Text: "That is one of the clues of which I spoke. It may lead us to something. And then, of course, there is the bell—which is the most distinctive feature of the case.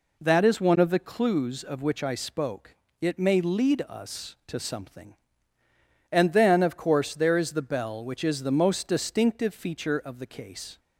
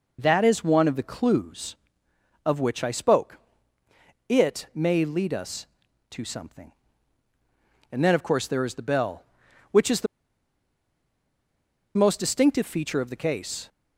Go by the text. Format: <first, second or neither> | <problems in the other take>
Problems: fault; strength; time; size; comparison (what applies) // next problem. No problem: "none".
first | pauses between "the" and "most"; strong; at 10.0 s; 1.8 s long